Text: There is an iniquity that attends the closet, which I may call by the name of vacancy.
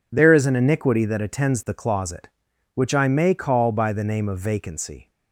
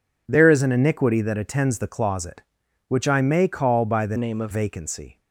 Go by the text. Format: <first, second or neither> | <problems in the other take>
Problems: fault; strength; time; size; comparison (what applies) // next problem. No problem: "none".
first | changes voice from "name" to "of"; from 4.1 to 4.5 s; 0.4 s long